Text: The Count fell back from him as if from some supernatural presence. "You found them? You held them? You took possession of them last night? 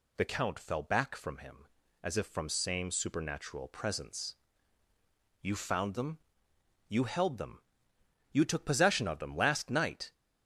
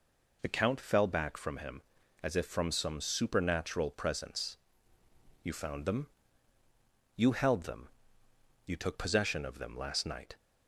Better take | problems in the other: second | says "same" for "some"; at 2.4 s

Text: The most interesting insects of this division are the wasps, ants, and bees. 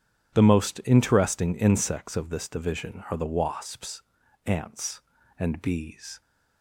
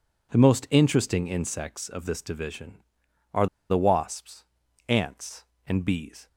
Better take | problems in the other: first | pauses between "are" and "the"; slight; at 3.4 s; 0.22 s long

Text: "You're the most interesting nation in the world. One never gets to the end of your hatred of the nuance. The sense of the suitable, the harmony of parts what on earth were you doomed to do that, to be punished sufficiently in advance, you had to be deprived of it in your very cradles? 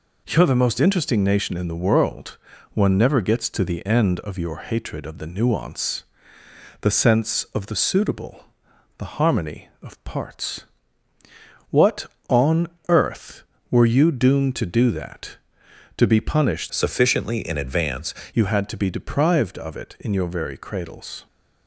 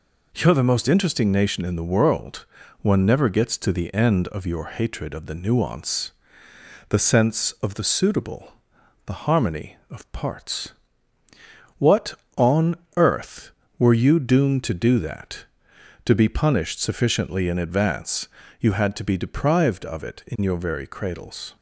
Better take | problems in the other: second | pauses between "parts" and "what"; at 10.6 s; 1.0 s long; also in the second // pauses between "on" and "earth"; slight; at 12.6 s; 0.18 s long; slight in the second // changes voice from "sufficiently" to "advance"; from 16.6 to 18.1 s; 1.5 s long

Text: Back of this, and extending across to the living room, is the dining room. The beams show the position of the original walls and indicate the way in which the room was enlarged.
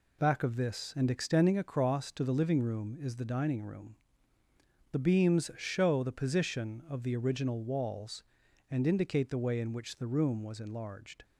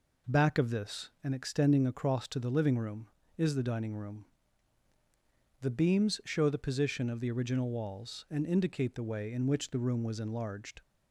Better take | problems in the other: neither | none

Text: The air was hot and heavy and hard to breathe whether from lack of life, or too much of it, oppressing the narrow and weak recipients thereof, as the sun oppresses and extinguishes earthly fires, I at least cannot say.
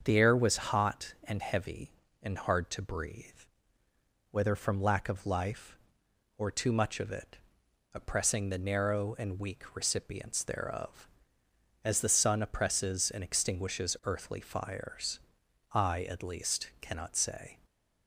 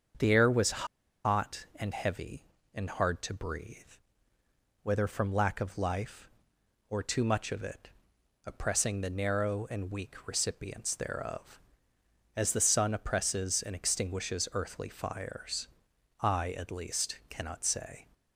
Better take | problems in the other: first | starts louder than the rest; until 1.5 s; 7 dB; also in the first // pauses between "was" and "hot"; at 0.8 s; 0.38 s long // pauses between "breathe" and "whether"; at 3.7 s; 1.0 s long; also in the first

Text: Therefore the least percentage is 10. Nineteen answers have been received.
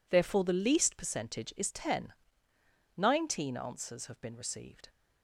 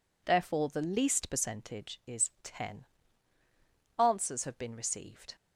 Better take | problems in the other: first | skips "Nineteen"; at 3.4 s

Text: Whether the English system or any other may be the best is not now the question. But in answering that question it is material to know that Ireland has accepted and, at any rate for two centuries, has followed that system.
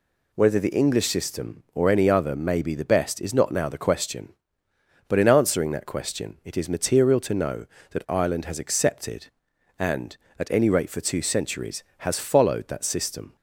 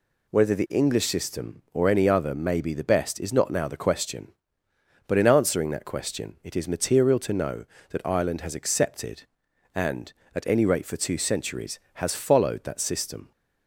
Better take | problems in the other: neither | none

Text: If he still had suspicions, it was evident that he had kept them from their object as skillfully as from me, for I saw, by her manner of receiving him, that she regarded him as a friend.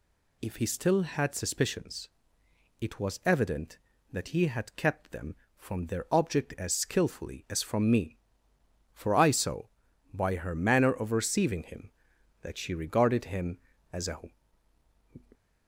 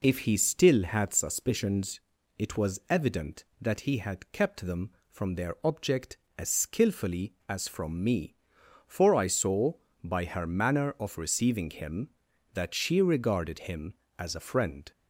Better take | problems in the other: second | stops before "friend"; at 15.3 s

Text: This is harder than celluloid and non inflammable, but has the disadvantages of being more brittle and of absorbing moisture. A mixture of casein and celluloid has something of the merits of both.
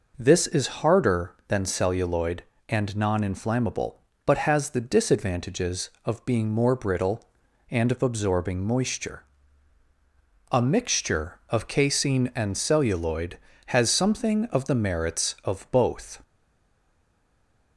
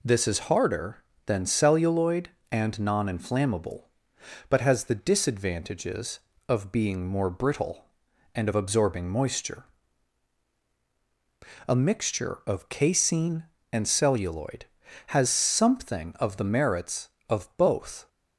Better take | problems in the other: second | stays silent after the last word; noticeable; from 16.2 s on; 1.5 s long

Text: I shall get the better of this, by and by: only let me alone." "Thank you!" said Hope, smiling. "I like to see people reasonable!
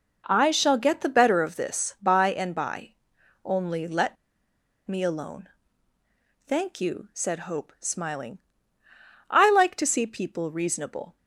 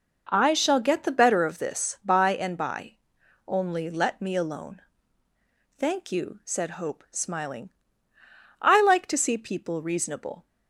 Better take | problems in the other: second | pauses between "let" and "me"; noticeable; at 4.1 s; 0.70 s long

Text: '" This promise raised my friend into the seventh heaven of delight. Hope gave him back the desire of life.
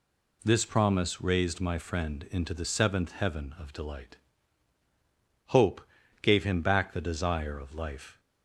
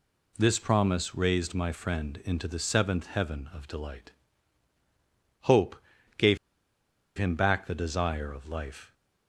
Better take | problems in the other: first | pauses between "Hope" and "gave"; at 5.7 s; 0.42 s long; also in the first // pauses between "gave" and "him"; noticeable; at 6.3 s; 0.79 s long

